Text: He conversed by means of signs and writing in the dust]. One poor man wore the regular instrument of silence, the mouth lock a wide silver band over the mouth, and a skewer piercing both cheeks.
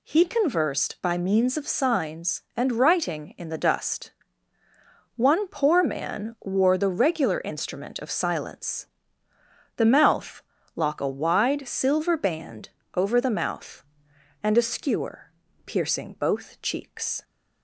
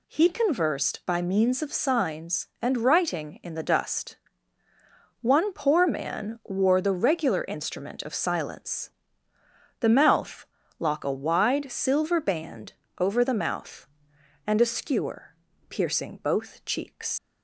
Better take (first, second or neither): first